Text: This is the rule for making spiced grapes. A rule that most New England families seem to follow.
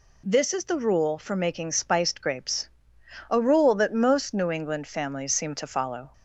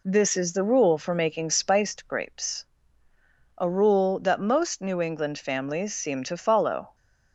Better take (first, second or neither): neither